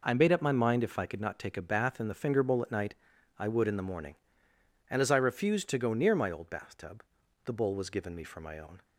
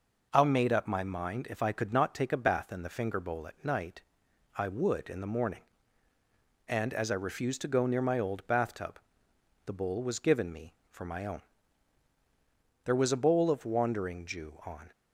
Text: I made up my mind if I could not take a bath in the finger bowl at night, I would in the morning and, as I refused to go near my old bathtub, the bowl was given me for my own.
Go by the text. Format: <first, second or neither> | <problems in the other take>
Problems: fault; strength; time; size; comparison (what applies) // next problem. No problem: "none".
first | goes on to say "There was a bowl of Wandering Jew on"; strong; from 12.8 s on; 2.0 s long